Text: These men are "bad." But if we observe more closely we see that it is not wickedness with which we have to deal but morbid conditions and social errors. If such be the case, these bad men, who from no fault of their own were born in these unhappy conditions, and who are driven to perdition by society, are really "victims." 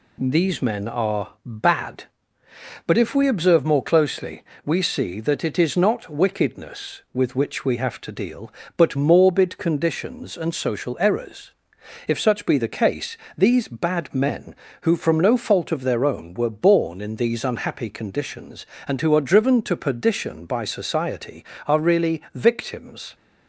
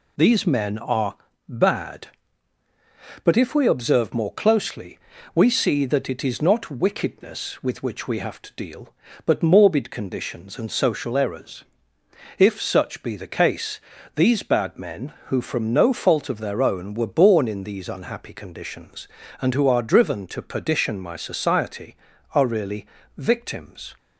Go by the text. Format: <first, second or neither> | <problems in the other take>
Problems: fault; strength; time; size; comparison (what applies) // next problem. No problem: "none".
first | pauses between "are" and "bad"; slight; at 1.1 s; 0.32 s long // pauses between "closely" and "we"; slight; at 4.9 s; 0.36 s long; slight in the first // says "my" for "by"; at 20.9 s // pauses between "really" and "victims"; slight; at 22.8 s; 0.32 s long